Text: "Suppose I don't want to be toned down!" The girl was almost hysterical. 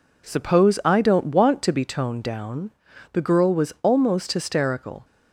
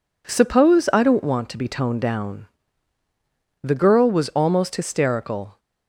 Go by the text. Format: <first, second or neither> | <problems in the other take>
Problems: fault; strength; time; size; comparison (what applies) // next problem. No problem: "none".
neither | none